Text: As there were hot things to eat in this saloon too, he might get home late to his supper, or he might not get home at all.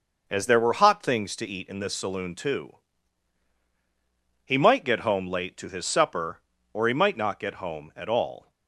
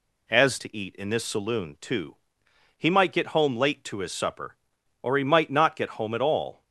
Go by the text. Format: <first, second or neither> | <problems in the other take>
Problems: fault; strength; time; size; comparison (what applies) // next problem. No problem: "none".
first | skips "there were hot things"; at 0.5 s